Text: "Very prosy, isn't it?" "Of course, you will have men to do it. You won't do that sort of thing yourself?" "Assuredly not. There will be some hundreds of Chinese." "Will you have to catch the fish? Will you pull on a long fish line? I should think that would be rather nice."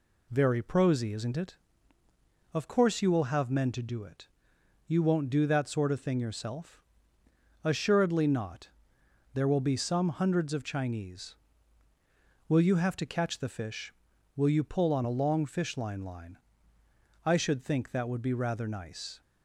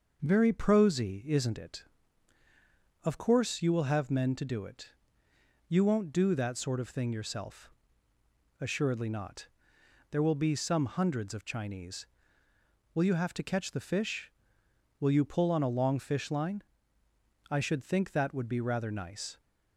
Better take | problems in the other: second | says "line" twice; at 16.0 s

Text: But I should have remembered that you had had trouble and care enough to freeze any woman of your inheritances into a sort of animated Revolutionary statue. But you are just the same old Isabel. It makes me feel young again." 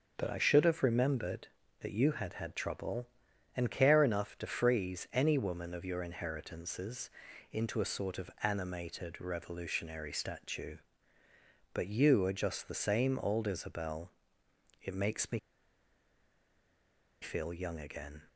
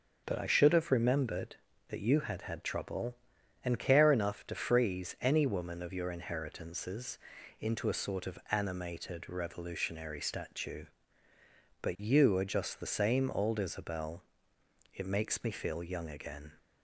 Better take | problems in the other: second | pauses between "inheritances" and "into"; at 7.0 s; 0.42 s long; also in the second // pauses between "me" and "feel"; strong; at 15.3 s; 1.8 s long

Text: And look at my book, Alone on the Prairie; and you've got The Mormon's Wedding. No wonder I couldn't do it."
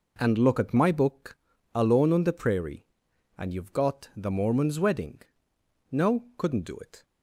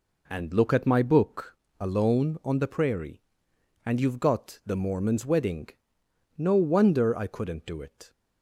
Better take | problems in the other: second | skips "wonder I"; at 6.2 s

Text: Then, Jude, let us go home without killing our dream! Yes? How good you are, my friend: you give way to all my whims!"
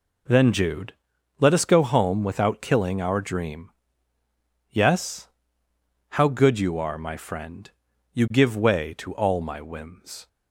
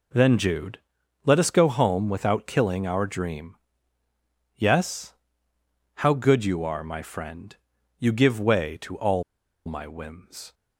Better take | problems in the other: first | pauses between "all" and "my"; at 9.2 s; 0.42 s long

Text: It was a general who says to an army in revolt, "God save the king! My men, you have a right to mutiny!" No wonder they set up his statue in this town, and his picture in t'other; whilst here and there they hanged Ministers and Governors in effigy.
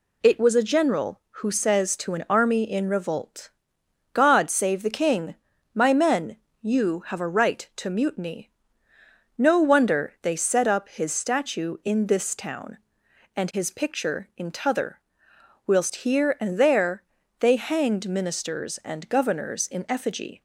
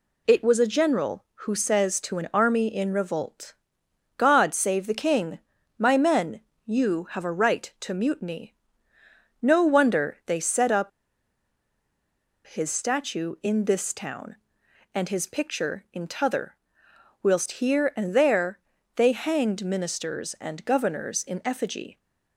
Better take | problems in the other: first | pauses between "up" and "his"; strong; at 10.9 s; 1.5 s long // pauses between "there" and "they"; slight; at 18.5 s; 0.36 s long; slight in the first

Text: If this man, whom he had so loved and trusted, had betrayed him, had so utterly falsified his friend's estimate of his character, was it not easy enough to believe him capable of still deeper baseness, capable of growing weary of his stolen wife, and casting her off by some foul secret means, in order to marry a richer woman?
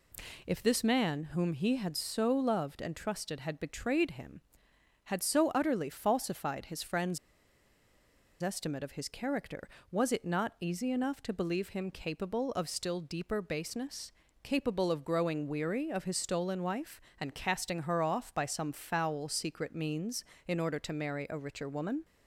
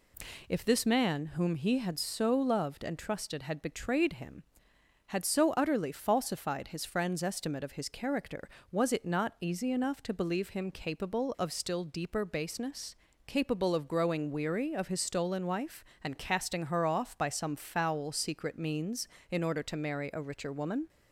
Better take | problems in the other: second | pauses between "friend's" and "estimate"; at 7.1 s; 1.2 s long

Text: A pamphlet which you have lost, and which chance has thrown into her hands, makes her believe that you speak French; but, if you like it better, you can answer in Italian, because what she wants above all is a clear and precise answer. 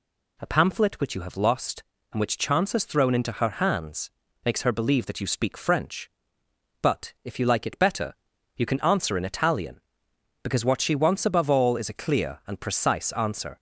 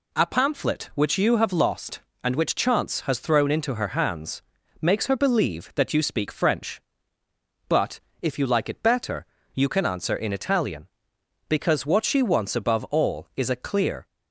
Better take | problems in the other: first | stops before "and precise answer"; at 14.0 s

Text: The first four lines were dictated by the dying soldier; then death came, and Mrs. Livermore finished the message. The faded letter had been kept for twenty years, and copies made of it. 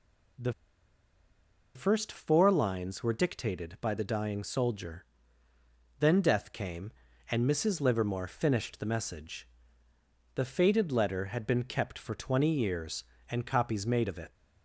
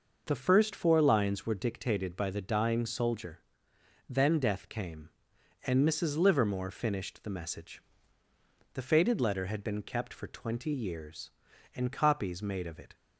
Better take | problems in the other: second | pauses between "The" and "first"; at 0.5 s; 1.2 s long

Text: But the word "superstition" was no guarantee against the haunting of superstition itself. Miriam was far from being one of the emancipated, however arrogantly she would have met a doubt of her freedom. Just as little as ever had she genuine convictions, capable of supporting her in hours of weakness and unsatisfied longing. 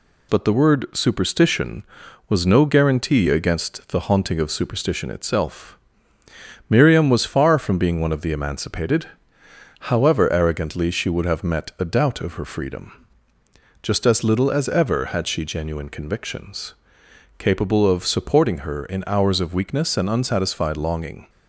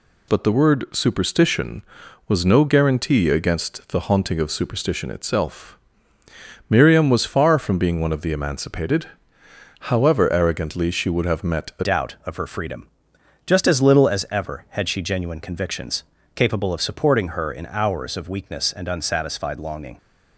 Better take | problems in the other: first | changes voice at "doubt"; from 11.8 s on; 8.1 s long

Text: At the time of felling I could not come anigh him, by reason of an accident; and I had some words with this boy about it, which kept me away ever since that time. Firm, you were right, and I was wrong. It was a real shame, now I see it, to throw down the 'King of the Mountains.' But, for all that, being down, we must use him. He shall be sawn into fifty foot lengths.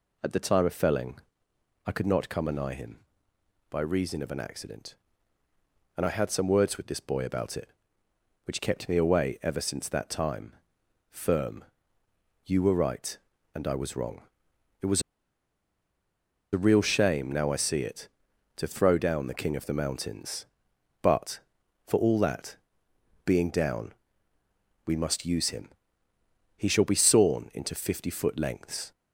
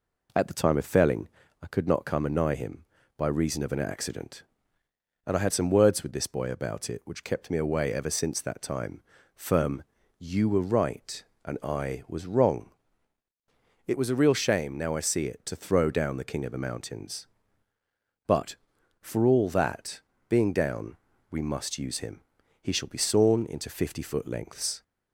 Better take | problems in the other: second | pauses between "felling" and "I"; noticeable; at 1.2 s; 0.66 s long; slight in the second // pauses between "was" and "a"; strong; at 15.0 s; 1.5 s long

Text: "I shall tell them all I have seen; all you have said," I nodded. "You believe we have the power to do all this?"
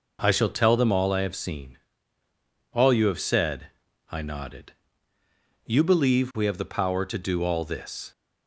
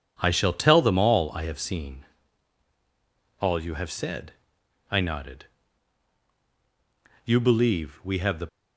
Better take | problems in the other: first | stops before "power to do all this"; at 8.4 s

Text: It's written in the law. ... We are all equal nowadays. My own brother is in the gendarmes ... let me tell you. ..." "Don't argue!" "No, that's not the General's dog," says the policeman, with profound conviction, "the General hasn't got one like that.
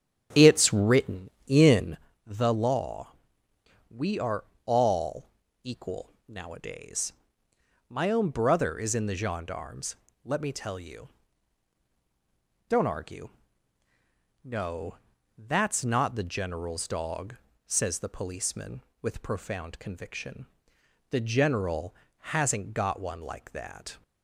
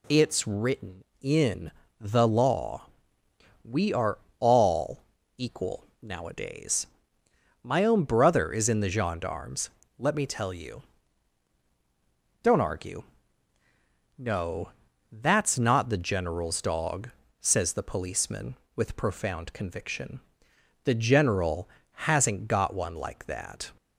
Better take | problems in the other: second | starts louder than the rest; strong; until 2.1 s; 10 dB // pauses between "in" and "the"; slight; at 1.9 s; 0.28 s long; slight in the second // pauses between "are" and "all"; slight; at 4.4 s; 0.20 s long; slight in the second // pauses between "all" and "equal"; at 5.2 s; 0.38 s long; also in the second // pauses between "General" and "hasn't"; slight; at 21.9 s; 0.24 s long; slight in the second

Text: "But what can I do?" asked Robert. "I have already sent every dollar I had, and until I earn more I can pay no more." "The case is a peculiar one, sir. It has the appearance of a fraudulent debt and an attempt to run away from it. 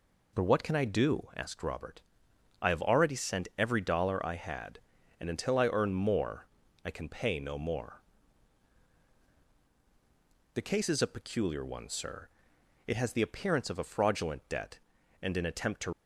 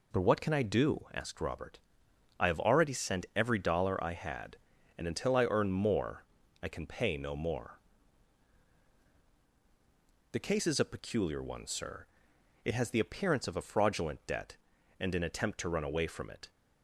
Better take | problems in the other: second | pauses between "more" and "I"; slight; at 6.4 s; 0.36 s long; slight in the second // stops before "run away from it"; at 15.9 s

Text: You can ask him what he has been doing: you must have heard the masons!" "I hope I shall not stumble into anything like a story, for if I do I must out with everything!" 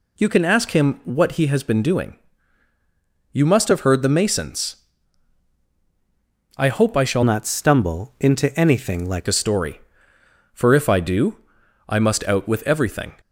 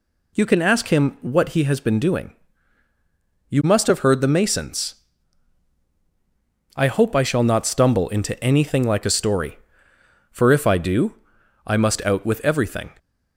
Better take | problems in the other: second | changes voice from "not" to "like"; from 7.2 to 9.2 s; 2.0 s long // pauses between "do" and "I"; noticeable; at 11.3 s; 0.50 s long; noticeable in the second

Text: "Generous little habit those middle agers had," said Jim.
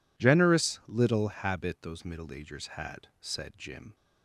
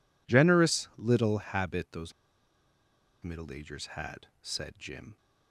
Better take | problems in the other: first | pauses between "those" and "middle"; at 2.1 s; 1.1 s long

